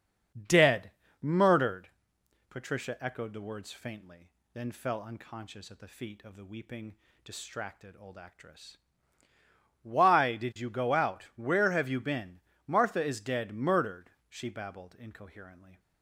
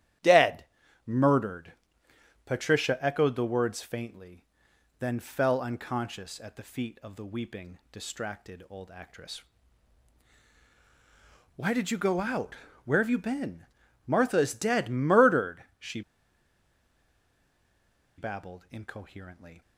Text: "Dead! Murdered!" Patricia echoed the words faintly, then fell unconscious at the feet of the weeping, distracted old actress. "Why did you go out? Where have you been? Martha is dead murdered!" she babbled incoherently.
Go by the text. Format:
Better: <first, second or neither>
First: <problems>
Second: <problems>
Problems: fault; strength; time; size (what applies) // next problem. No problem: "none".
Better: first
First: starts louder than the rest; until 1.8 s; 7 dB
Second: starts louder than the rest; strong; until 1.6 s; 11.5 dB // pauses between "she" and "babbled"; strong; at 16.0 s; 2.1 s long